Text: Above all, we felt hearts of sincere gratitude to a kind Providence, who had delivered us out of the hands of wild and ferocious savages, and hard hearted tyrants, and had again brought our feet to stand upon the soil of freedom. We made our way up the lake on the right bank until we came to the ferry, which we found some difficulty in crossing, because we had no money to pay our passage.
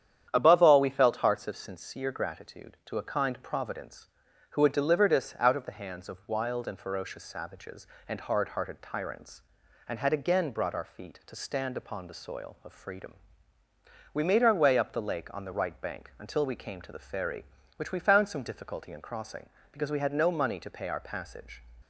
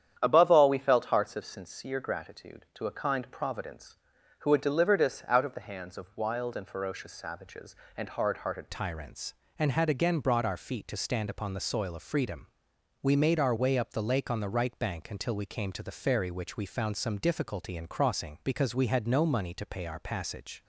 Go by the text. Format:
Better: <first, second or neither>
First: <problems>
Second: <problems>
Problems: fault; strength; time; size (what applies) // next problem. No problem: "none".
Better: first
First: starts louder than the rest; strong; until 1.3 s; 9.5 dB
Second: starts louder than the rest; strong; until 1.2 s; 9.5 dB // changes voice at "tyrants"; from 8.7 s on; 11.9 s long